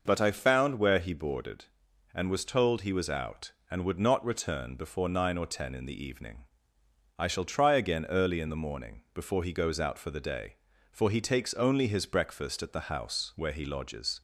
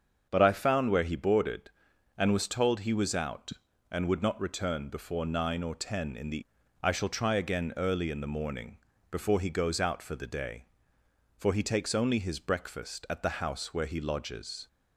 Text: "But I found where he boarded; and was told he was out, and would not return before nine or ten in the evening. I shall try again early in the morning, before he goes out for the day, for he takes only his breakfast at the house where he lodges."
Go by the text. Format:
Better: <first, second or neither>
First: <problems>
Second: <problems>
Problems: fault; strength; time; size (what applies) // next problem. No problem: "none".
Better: first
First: none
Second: starts louder than the rest; until 1.3 s; 7 dB // skips "evening"; at 6.6 s